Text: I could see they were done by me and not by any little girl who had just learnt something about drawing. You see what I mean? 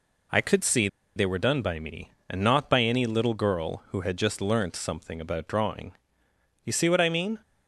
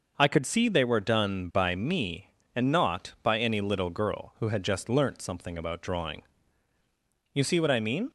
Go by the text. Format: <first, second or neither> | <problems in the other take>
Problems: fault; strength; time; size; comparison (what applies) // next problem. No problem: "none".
second | pauses between "see" and "they"; slight; at 0.8 s; 0.28 s long